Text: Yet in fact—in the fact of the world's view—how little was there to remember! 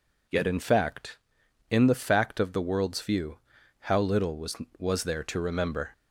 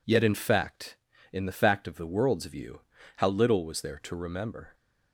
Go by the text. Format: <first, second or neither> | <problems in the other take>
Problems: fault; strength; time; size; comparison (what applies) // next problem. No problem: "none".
second | says "was" twice; at 4.7 s